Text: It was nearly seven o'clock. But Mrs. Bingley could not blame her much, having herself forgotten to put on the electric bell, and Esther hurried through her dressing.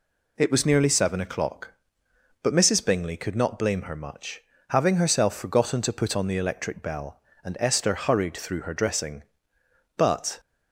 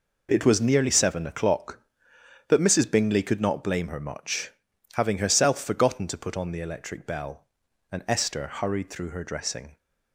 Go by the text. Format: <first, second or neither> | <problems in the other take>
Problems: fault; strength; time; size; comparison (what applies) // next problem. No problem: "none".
second | goes on to say "But"; slight; from 9.9 s on; 0.44 s long